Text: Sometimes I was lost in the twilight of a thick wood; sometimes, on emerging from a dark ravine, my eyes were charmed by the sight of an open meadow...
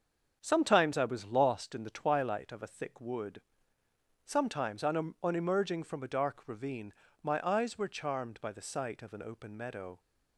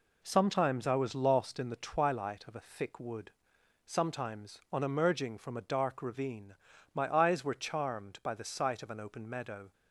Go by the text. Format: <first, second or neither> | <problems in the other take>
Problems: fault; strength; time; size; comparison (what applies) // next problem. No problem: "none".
second | starts louder than the rest; until 1.4 s; 7 dB // says "on" twice; at 5.2 s